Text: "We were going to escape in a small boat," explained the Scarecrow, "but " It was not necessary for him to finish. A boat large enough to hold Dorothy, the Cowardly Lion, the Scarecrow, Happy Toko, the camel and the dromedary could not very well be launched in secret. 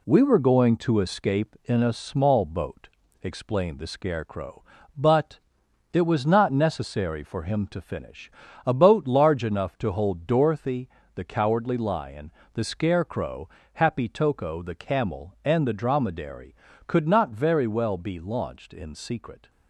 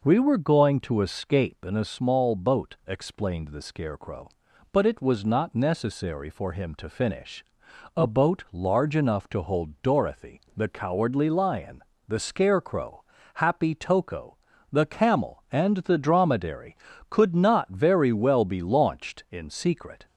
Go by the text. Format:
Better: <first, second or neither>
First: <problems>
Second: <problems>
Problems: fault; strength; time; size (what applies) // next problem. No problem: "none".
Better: second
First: gets quieter; slight; throughout; 3 dB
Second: none